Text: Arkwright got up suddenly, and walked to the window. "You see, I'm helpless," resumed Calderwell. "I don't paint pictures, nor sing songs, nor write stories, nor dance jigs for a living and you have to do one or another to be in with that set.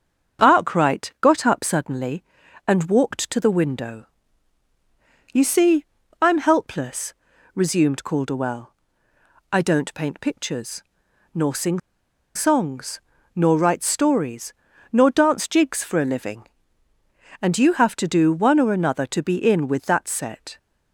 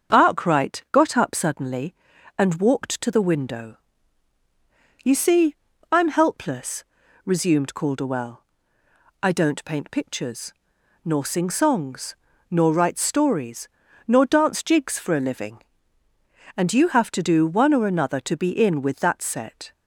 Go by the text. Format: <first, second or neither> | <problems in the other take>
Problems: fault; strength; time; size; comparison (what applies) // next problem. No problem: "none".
second | starts louder than the rest; strong; until 1.4 s; 7.5 dB; strong in the second // pauses between "sing" and "songs"; noticeable; at 11.7 s; 0.57 s long